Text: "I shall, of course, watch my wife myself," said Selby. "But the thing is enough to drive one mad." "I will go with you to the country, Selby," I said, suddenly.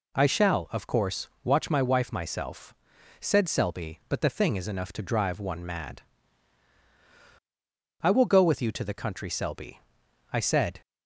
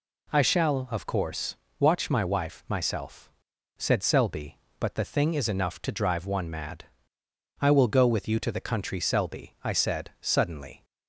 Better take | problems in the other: second | stops before "suddenly"; at 10.8 s

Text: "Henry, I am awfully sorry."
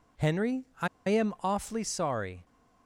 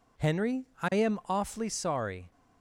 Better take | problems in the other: second | pauses between "I" and "am"; slight; at 0.8 s; 0.20 s long

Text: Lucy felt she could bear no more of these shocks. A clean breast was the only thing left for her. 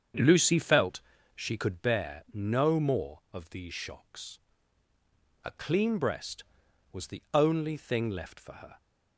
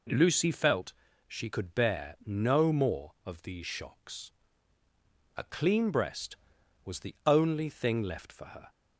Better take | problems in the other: second | starts louder than the rest; strong; until 1.8 s; 7.5 dB // pauses between "felt" and "she"; slight; at 1.0 s; 0.34 s long; slight in the second

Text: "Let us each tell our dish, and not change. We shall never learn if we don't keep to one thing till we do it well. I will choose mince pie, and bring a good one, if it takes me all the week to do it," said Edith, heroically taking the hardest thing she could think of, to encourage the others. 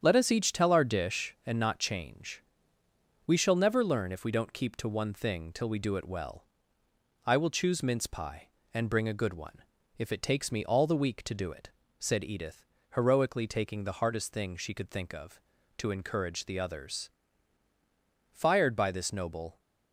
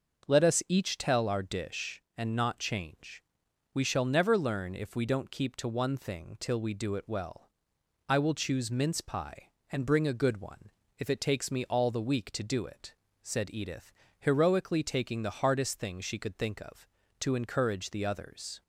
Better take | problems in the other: second | starts louder than the rest; strong; until 1.0 s; 8.5 dB; noticeable in the second // goes on to say "Fired by this noble"; noticeable; from 18.3 s on; 1.2 s long

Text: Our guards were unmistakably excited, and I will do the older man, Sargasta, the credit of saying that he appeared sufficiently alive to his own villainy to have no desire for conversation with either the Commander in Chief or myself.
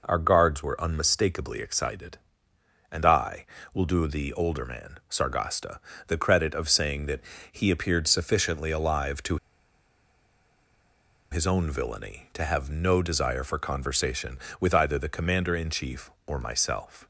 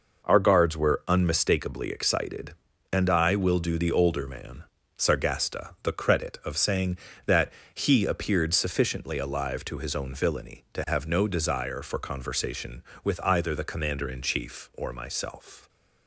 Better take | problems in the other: second | pauses between "that" and "he"; slight; at 7.2 s; 0.30 s long; slight in the second // pauses between "to" and "his"; strong; at 9.3 s; 1.9 s long

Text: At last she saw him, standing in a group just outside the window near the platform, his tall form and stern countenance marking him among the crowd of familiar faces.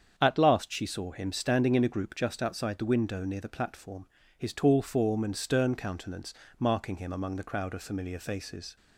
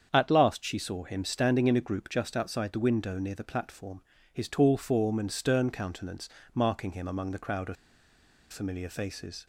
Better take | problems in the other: first | starts louder than the rest; strong; until 1.1 s; 7.5 dB; strong in the first // pauses between "countenance" and "marking"; slight; at 6.2 s; 0.26 s long; slight in the first // pauses between "of" and "familiar"; noticeable; at 7.7 s; 0.76 s long

